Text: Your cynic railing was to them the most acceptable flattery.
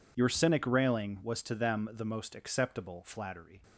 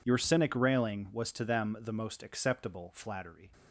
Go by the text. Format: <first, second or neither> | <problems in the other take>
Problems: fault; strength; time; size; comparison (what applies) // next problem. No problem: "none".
neither | none